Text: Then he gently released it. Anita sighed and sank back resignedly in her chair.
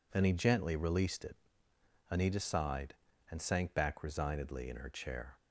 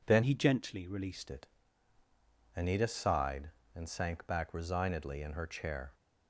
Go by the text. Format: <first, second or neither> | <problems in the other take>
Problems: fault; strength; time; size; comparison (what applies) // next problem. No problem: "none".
first | changes voice from "he" to "released"; from 0.2 to 1.2 s; 1.0 s long